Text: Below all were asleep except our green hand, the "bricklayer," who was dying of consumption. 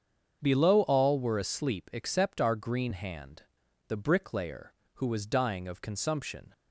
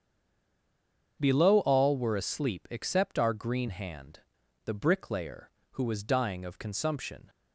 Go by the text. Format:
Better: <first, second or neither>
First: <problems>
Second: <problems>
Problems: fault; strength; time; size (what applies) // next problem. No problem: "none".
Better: first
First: starts louder than the rest; strong; until 1.4 s; 7 dB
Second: stays silent before the first word; noticeable; until 1.1 s; 1.1 s long // starts louder than the rest; strong; until 2.2 s; 7 dB